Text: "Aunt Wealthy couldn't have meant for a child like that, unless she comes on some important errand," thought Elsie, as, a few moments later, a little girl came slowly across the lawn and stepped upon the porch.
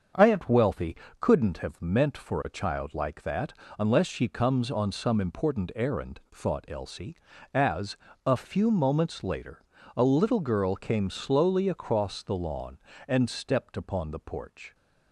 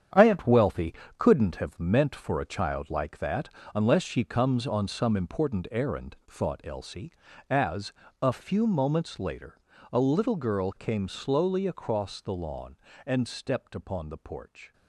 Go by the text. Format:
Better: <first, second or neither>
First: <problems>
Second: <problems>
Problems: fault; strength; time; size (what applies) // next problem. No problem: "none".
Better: first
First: starts louder than the rest; until 1.4 s; 7 dB // pauses between "Wealthy" and "couldn't"; slight; at 0.9 s; 0.24 s long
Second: gets quieter; strong; throughout; 9.5 dB // starts louder than the rest; strong; until 1.3 s; 9 dB // pauses between "Wealthy" and "couldn't"; slight; at 0.9 s; 0.24 s long